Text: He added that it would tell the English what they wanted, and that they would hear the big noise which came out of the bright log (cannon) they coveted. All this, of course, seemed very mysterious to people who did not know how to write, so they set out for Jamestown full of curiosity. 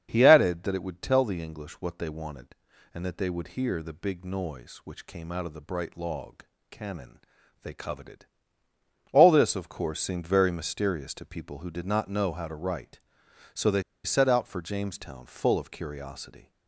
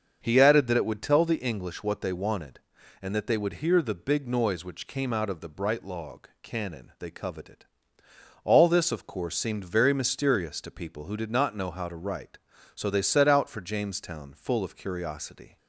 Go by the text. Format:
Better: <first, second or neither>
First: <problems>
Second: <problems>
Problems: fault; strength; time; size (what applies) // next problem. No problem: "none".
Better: second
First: starts louder than the rest; strong; until 1.1 s; 7 dB // pauses between "they" and "set"; slight; at 13.8 s; 0.22 s long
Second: starts louder than the rest; until 1.2 s; 6.5 dB